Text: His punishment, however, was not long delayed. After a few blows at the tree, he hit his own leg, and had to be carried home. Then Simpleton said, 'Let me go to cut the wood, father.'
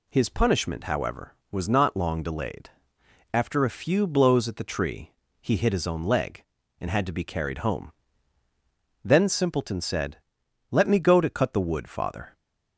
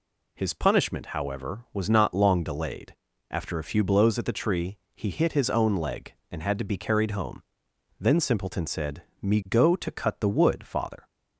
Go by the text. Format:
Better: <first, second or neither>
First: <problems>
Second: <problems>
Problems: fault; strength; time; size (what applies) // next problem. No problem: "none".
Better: first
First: none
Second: skips "Let"; at 9.1 s